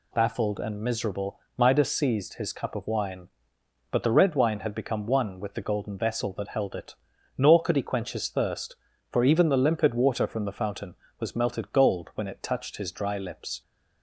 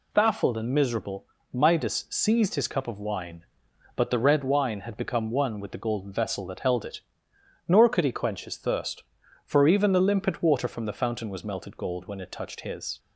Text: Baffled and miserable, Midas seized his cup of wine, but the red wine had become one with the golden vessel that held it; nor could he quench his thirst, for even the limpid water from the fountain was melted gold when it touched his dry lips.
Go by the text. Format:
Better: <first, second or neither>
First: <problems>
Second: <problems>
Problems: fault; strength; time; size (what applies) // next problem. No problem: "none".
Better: first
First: none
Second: stops before "dry lips"; at 12.9 s